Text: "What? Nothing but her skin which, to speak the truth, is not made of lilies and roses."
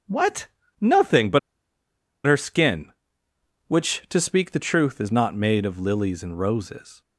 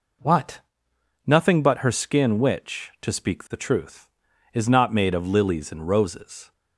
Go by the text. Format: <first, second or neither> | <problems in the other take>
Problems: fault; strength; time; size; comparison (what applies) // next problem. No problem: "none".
second | pauses between "but" and "her"; noticeable; at 1.3 s; 0.87 s long